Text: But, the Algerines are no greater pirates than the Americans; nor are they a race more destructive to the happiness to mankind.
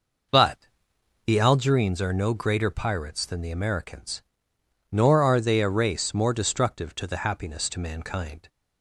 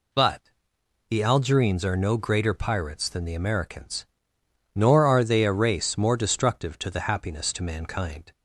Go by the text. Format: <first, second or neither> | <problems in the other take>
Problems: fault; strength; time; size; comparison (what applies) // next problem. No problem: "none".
second | starts louder than the rest; noticeable; until 1.6 s; 5.5 dB